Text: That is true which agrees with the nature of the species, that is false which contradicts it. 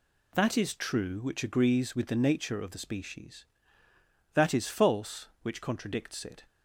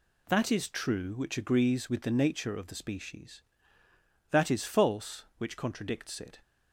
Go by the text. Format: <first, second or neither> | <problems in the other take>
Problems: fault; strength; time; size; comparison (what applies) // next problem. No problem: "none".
neither | none